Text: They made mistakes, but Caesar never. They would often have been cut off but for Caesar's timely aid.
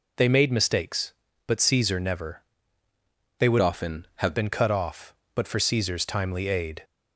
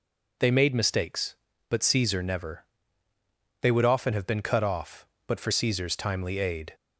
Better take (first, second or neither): second